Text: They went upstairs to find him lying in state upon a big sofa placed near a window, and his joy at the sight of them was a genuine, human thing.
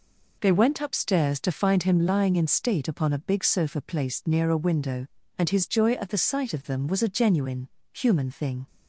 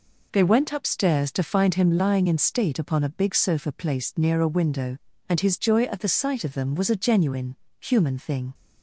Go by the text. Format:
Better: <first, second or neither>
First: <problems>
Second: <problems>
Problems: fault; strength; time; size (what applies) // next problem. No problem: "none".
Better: neither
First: none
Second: none